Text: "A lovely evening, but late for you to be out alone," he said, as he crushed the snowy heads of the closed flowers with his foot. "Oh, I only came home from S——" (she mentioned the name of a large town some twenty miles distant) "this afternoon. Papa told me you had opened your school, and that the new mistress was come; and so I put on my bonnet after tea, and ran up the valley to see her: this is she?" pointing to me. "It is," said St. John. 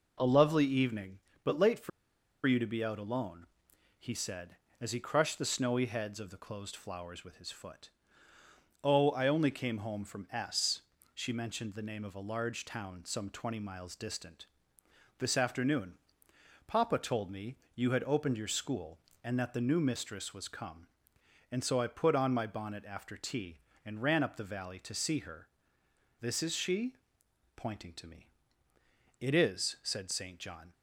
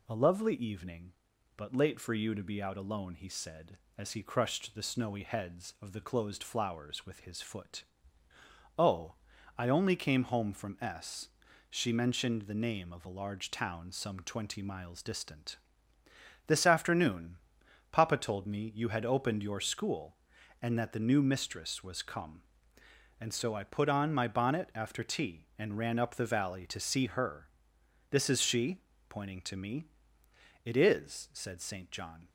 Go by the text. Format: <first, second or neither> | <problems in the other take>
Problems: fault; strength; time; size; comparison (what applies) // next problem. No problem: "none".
second | pauses between "for" and "you"; noticeable; at 1.8 s; 0.56 s long // pauses between "me" and "you"; slight; at 17.5 s; 0.16 s long